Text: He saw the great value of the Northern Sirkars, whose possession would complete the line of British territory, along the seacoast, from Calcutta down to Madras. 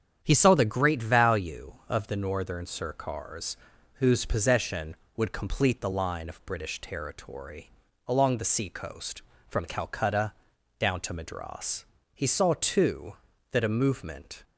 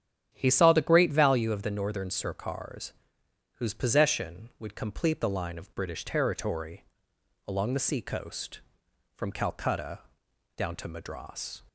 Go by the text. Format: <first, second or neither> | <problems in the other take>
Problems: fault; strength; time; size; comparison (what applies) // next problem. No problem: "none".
second | starts louder than the rest; strong; until 1.2 s; 8.5 dB; strong in the second // pauses between "Calcutta" and "down"; noticeable; at 10.3 s; 0.46 s long; noticeable in the second // goes on to say "He saw too that a movement"; strong; from 12.1 s on; 2.3 s long